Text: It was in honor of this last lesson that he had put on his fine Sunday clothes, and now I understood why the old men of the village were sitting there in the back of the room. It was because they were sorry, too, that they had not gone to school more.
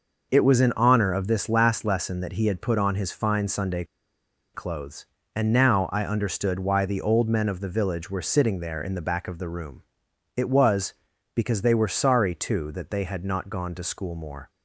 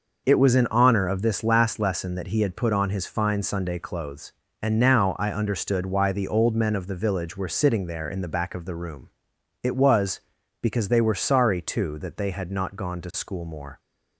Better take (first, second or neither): second